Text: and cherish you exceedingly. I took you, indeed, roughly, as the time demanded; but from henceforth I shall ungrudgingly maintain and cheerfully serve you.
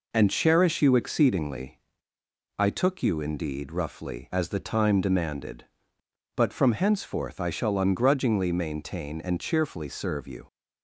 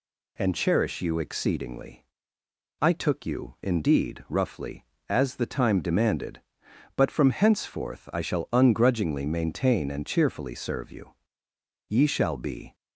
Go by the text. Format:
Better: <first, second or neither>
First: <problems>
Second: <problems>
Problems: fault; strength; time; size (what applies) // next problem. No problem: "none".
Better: first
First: none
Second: goes on to say "Ye shall be"; noticeable; from 11.8 s on; 0.86 s long